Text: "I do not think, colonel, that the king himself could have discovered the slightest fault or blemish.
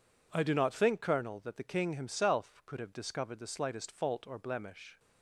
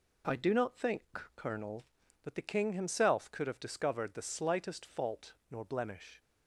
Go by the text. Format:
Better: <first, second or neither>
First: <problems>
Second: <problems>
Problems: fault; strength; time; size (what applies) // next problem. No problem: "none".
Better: first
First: none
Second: says "nor" for "or"; at 5.5 s